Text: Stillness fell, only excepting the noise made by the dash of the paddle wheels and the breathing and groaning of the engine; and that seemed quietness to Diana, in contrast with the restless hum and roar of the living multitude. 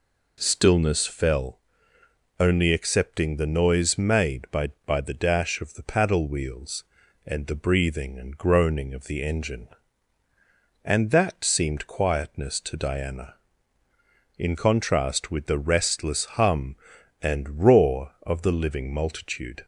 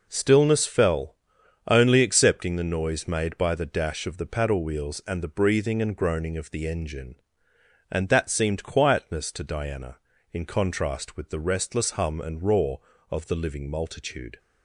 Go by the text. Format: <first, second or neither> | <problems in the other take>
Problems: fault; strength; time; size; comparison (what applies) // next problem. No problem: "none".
second | says "by" twice; at 4.8 s